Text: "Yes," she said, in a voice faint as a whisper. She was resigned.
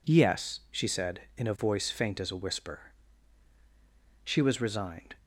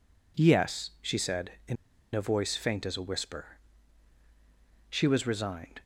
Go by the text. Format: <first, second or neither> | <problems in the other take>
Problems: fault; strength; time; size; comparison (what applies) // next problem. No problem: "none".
first | pauses between "in" and "a"; at 1.7 s; 0.38 s long